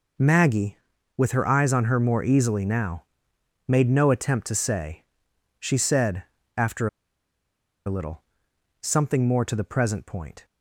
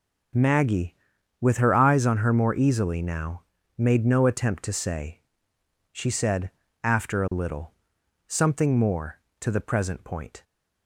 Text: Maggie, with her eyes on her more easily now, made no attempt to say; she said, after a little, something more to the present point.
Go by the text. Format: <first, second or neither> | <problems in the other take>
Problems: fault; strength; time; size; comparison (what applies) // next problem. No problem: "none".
second | pauses between "after" and "a"; at 6.8 s; 0.99 s long